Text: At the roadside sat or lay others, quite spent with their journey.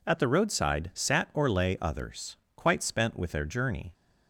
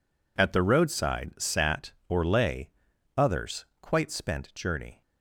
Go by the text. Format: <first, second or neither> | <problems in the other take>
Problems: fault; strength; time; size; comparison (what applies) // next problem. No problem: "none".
first | pauses between "lay" and "others"; noticeable; at 2.6 s; 0.48 s long // skips "with their"; at 4.5 s